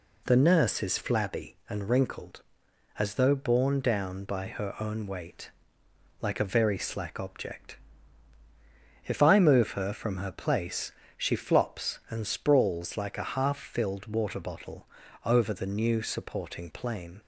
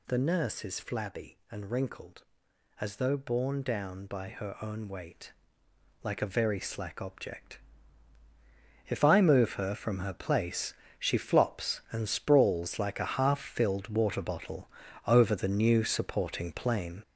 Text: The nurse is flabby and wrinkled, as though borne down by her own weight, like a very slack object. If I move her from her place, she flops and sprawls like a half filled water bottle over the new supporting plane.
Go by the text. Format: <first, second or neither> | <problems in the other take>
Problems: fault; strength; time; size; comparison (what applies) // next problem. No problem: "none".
first | gets louder; strong; throughout; 7 dB // pauses between "bottle" and "over"; at 14.6 s; 0.38 s long; also in the first